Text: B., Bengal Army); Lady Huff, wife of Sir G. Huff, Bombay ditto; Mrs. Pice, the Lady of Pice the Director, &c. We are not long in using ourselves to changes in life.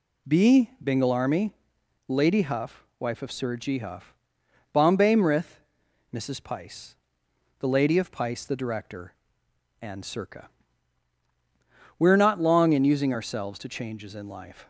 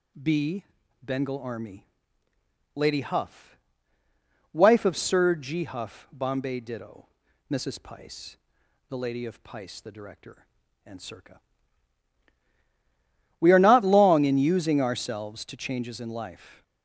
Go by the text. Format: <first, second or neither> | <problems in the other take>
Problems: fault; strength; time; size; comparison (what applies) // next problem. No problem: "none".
second | says "mrith" for "ditto"; at 5.1 s